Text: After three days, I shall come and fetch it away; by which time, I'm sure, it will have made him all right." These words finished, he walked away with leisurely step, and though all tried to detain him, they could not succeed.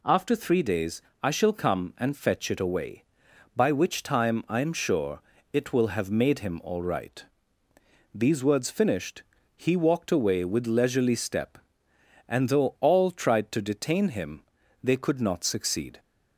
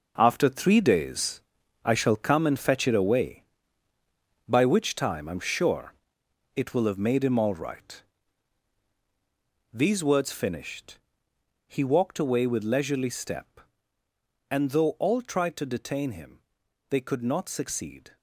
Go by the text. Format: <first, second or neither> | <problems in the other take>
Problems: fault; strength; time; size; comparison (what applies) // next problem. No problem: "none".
first | gets quieter; strong; throughout; 10 dB